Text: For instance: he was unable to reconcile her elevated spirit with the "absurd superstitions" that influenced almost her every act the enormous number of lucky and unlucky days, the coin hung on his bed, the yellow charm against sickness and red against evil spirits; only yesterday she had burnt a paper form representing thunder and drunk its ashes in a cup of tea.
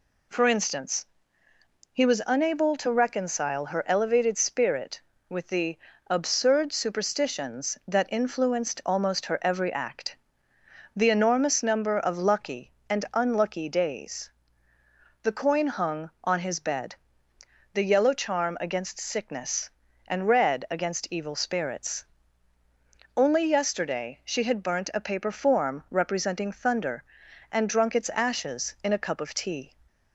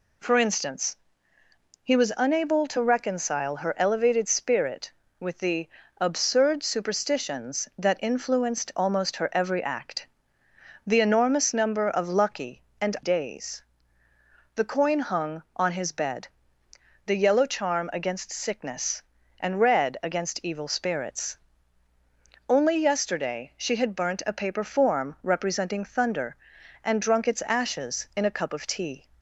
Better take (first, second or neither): first